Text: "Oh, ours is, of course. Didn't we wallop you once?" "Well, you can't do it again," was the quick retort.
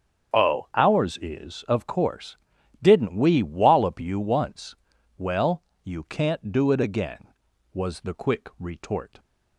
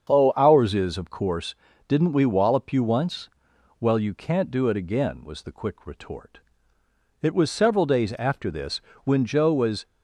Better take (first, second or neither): first